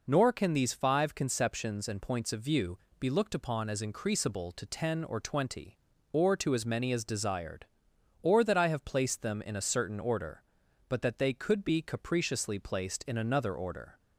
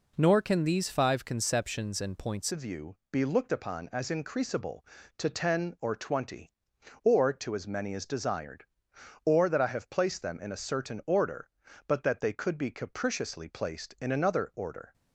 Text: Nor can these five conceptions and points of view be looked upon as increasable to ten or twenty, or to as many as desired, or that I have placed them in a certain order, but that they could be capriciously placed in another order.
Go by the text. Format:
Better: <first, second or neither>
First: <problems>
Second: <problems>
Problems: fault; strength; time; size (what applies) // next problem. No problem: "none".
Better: first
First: pauses between "view" and "be"; slight; at 2.7 s; 0.20 s long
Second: changes voice at "of"; from 2.5 s on; 12.4 s long // pauses between "view" and "be"; slight; at 2.9 s; 0.16 s long